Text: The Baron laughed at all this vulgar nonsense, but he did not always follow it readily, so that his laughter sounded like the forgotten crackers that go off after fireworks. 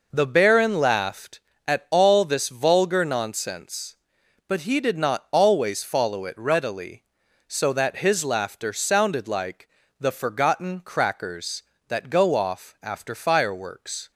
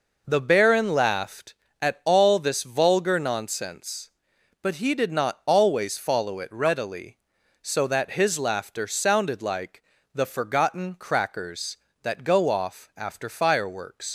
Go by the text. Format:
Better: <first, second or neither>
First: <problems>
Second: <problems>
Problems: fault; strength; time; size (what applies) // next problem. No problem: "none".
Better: first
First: pauses between "like" and "the"; slight; at 9.6 s; 0.32 s long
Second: pauses between "like" and "the"; slight; at 9.8 s; 0.32 s long // leaves "fireworks" unfinished; at 14.0 s; 100 ms